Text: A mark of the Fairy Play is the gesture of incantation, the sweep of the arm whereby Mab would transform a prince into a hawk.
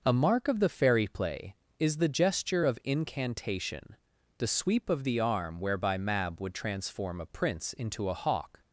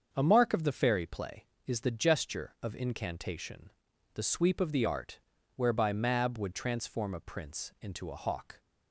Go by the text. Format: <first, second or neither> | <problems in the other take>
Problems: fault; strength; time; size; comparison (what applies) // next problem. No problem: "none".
first | starts louder than the rest; until 1.1 s; 7 dB // says "art" for "arm"; at 4.8 s